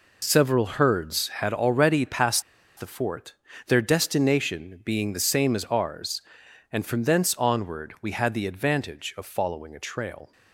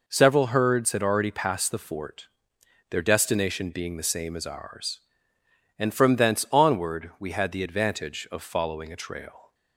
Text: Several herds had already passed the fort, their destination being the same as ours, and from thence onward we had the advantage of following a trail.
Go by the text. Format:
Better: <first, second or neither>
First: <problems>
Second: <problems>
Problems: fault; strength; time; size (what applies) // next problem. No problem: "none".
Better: second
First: pauses between "passed" and "the"; at 2.4 s; 0.37 s long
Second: none